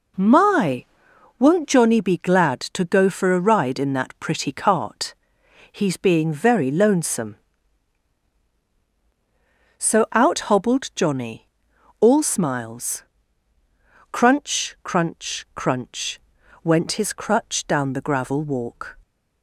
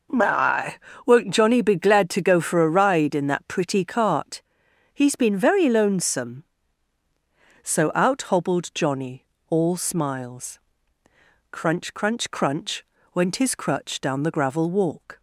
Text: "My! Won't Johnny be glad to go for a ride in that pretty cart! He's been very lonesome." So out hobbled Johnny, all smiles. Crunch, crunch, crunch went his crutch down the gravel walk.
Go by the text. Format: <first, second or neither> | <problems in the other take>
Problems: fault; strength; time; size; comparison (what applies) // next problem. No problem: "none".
second | says "being" for "been"; at 5.9 s // pauses between "crunch" and "went"; at 16.1 s; 0.44 s long; slight in the second